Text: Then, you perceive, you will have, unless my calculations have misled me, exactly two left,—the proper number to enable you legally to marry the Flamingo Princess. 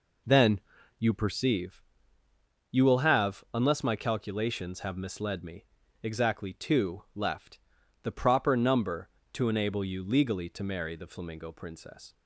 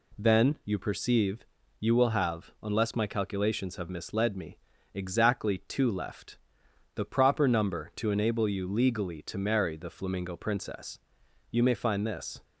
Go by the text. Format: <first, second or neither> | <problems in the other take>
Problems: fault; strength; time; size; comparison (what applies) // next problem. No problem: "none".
first | goes on to say "You may find this"; noticeable; from 11.5 s on; 0.92 s long